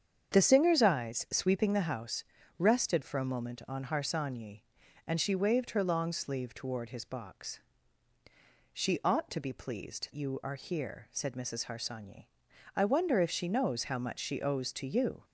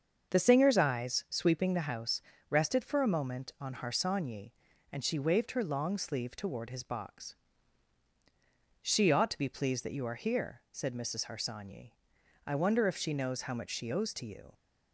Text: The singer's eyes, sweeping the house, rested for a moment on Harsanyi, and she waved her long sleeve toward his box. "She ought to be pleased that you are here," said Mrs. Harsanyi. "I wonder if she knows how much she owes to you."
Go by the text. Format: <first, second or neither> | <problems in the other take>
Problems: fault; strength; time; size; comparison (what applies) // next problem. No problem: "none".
second | starts louder than the rest; strong; until 1.3 s; 7.5 dB; also in the second // skips "that"; at 10.1 s